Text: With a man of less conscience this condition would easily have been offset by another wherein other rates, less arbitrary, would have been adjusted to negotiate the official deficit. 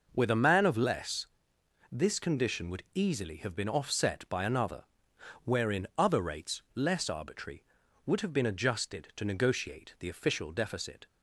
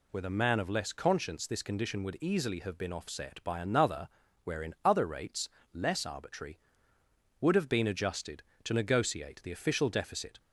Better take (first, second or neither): second